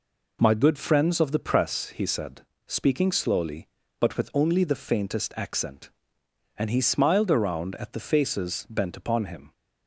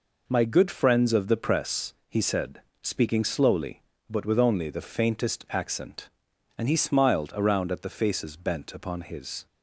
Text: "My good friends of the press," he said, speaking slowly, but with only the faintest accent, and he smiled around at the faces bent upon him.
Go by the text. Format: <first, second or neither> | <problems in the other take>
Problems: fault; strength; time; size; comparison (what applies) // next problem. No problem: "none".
first | says "his" for "him"; at 9.0 s